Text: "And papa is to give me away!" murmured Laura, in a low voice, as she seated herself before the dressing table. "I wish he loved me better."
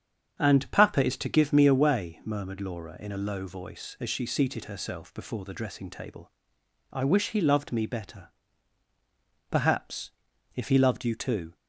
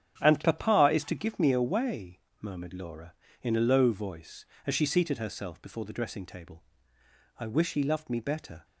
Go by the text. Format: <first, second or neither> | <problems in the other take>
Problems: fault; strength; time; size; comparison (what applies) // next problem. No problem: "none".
second | starts louder than the rest; strong; until 1.3 s; 8 dB; strong in the second // goes on to say "Perhaps if he loved you too"; strong; from 9.4 s on; 2.0 s long